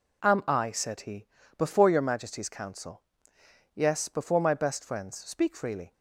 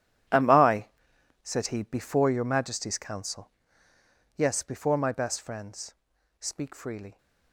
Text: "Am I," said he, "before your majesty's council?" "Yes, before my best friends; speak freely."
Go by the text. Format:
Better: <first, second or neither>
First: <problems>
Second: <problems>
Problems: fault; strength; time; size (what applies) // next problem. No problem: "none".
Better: first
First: none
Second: gets quieter; strong; throughout; 14 dB